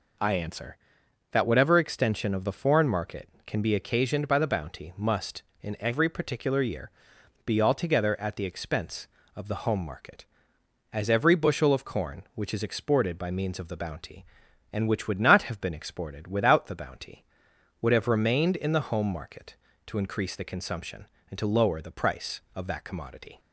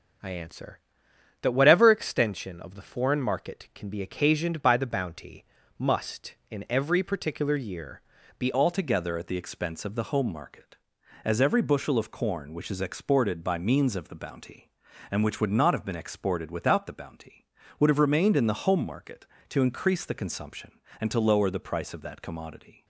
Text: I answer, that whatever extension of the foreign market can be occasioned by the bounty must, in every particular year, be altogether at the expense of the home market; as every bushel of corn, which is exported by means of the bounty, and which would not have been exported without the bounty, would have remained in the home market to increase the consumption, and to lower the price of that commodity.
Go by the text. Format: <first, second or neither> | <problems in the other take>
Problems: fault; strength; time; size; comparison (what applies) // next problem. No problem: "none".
first | starts louder than the rest; noticeable; until 1.8 s; 6 dB // pauses between "bounty" and "must"; slight; at 5.4 s; 0.34 s long // changes voice at "altogether"; from 8.5 s on; 14.3 s long